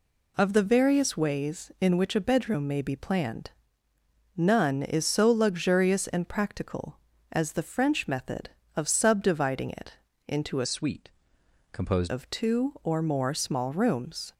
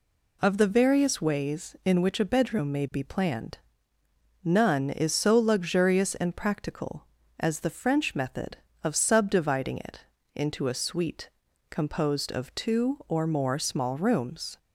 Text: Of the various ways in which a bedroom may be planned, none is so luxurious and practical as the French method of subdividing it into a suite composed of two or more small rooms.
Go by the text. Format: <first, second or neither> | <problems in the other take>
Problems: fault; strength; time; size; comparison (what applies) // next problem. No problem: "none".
second | pauses between "it" and "into"; slight; at 9.9 s; 0.34 s long; slight in the second // changes voice from "suite" to "composed"; from 10.6 to 12.1 s; 1.5 s long // pauses between "suite" and "composed"; noticeable; at 11.0 s; 0.64 s long; also in the second